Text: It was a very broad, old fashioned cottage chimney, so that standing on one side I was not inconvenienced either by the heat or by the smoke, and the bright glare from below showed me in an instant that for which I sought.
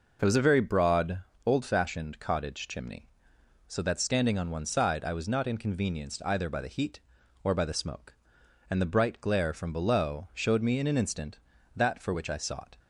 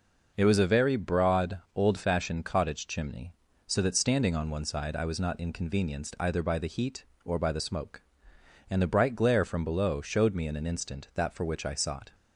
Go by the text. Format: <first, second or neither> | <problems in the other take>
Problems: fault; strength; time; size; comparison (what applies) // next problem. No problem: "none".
neither | none